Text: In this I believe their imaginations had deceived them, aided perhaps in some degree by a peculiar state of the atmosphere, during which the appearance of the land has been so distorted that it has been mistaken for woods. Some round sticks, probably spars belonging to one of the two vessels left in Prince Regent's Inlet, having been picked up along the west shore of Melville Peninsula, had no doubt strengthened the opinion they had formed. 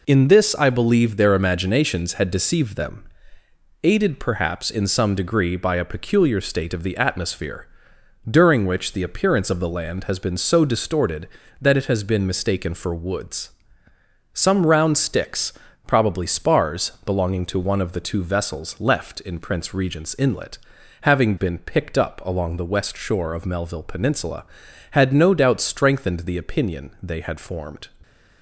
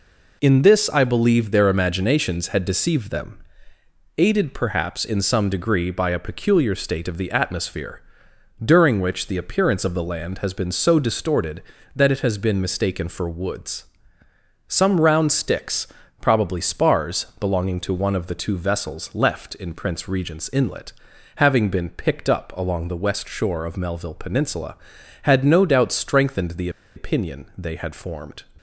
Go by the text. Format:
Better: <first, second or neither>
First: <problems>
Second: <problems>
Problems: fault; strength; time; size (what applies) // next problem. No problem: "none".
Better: first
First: none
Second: pauses between "the" and "opinion"; slight; at 26.6 s; 0.26 s long